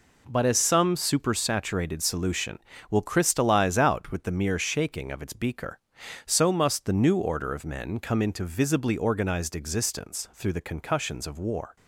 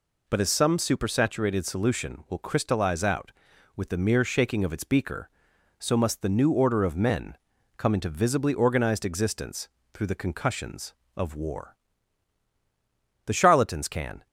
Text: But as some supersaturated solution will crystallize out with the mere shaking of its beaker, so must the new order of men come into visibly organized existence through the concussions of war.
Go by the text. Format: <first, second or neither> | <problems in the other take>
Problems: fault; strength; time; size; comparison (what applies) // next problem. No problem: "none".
first | pauses between "men" and "come"; at 7.3 s; 0.40 s long // pauses between "existence" and "through"; slight; at 9.6 s; 0.24 s long // goes on to say "The charlatans can"; noticeable; from 13.2 s on; 1.0 s long